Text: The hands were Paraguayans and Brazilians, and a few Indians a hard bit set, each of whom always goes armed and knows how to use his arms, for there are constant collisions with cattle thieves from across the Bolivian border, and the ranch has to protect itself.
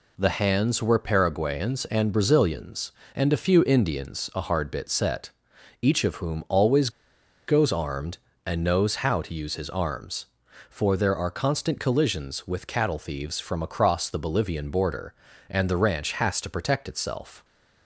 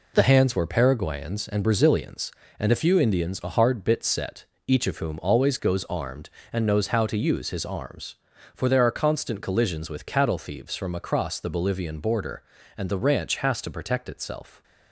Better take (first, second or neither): second